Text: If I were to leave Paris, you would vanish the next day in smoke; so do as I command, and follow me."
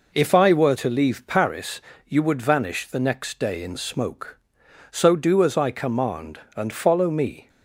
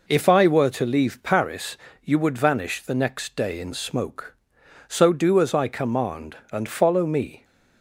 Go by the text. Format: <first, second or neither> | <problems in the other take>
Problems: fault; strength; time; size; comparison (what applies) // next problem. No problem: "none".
neither | none